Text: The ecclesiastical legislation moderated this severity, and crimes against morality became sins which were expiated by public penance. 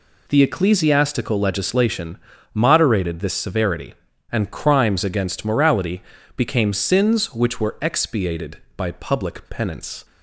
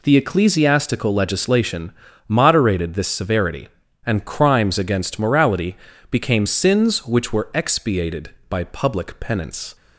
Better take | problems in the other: neither | pauses between "legislation" and "moderated"; slight; the same in both // pauses between "morality" and "became"; slight; the same in both

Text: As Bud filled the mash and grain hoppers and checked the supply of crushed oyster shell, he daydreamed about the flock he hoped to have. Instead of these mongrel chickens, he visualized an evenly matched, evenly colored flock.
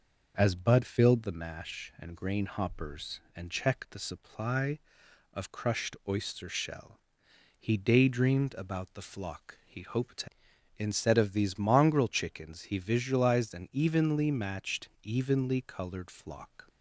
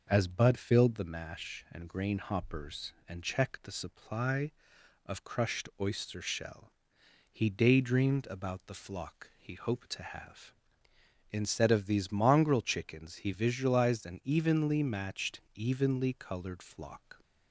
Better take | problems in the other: second | skips "have"; at 10.5 s

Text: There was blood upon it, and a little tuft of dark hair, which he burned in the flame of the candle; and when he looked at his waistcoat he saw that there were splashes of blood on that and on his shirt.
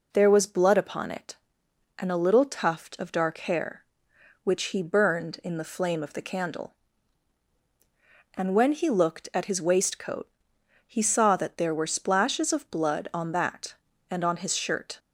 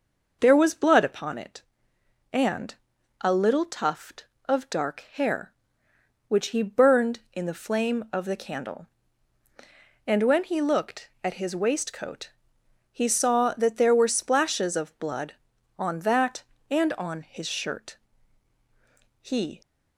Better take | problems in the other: first | pauses between "and" and "a"; noticeable; at 2.7 s; 0.48 s long // pauses between "waistcoat" and "he"; noticeable; at 12.3 s; 0.62 s long; noticeable in the first // goes on to say "He"; slight; from 19.2 s on; 0.40 s long

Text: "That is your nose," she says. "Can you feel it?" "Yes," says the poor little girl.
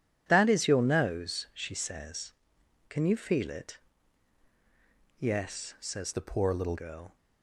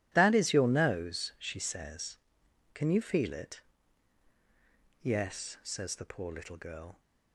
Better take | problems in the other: second | changes voice from "the" to "little"; from 6.1 to 6.7 s; 0.6 s long

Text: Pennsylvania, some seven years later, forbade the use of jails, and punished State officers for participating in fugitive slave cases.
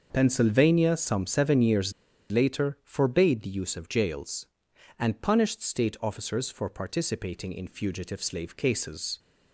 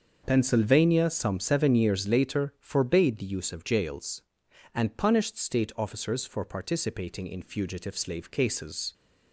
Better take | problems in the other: second | starts louder than the rest; until 1.1 s; 6.5 dB; also in the second // pauses between "years" and "later"; at 1.9 s; 0.40 s long

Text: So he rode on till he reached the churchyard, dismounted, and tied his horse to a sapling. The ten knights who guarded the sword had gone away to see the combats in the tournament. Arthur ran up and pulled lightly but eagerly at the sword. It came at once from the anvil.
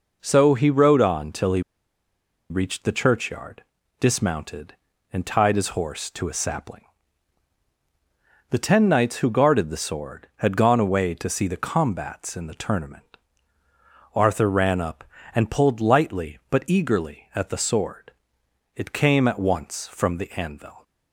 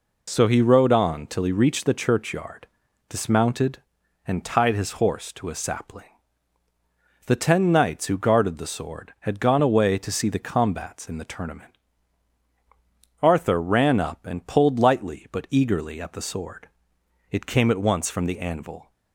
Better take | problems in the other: second | pauses between "he" and "reached"; noticeable; at 1.6 s; 0.88 s long

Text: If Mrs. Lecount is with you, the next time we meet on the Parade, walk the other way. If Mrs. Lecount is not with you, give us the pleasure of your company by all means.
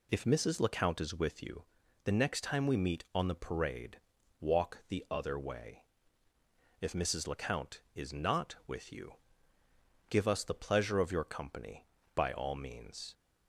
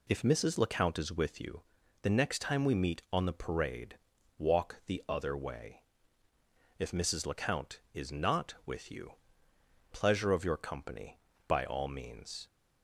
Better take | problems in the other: first | skips "give us the"; at 9.5 s

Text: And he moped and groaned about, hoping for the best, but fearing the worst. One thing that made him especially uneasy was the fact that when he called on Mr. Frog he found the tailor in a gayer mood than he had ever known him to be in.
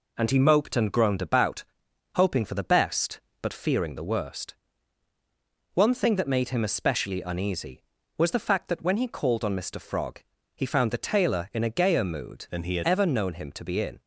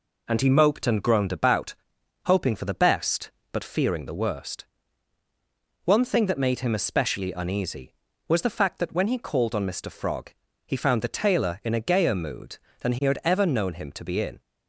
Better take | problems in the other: second | pauses between "Frog" and "he"; slight; at 10.1 s; 0.34 s long; slight in the second // changes voice from "than" to "had"; from 12.5 to 12.8 s; 0.3 s long

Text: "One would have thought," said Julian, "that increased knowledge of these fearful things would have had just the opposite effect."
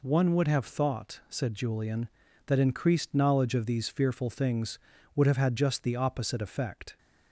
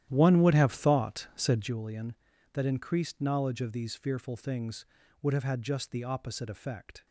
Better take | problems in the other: first | starts louder than the rest; strong; until 1.8 s; 11.5 dB

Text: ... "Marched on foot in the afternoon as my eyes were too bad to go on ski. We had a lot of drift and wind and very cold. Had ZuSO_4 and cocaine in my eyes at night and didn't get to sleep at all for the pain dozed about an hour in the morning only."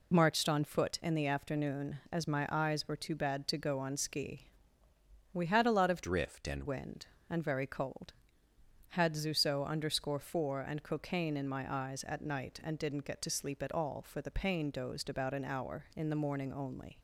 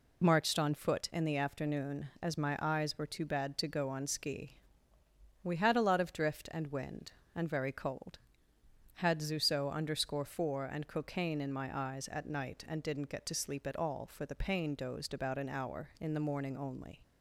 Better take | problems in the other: second | changes voice from "drift" to "and"; from 6.0 to 6.6 s; 0.6 s long

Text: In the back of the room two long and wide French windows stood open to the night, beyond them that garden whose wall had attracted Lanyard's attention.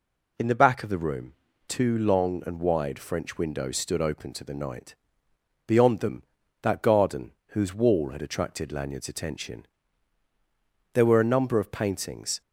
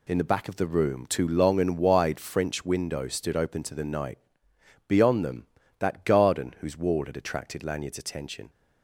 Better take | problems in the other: second | pauses between "room" and "two"; slight; at 1.3 s; 0.34 s long // pauses between "garden" and "whose"; slight; at 7.3 s; 0.18 s long // goes on to say "There were a number of paintings"; from 10.9 s on; 1.4 s long

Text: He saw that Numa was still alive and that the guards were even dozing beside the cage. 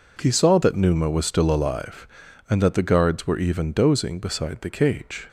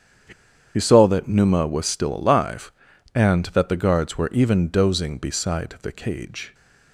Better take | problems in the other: first | starts louder than the rest; strong; until 1.7 s; 8 dB // pauses between "He" and "saw"; at 0.3 s; 0.44 s long

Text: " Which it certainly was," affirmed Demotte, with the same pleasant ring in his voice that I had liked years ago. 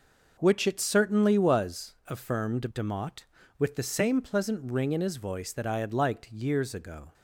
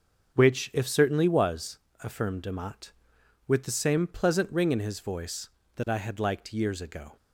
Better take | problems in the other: first | starts louder than the rest; until 1.4 s; 6.5 dB // says "if" for "it"; at 0.7 s

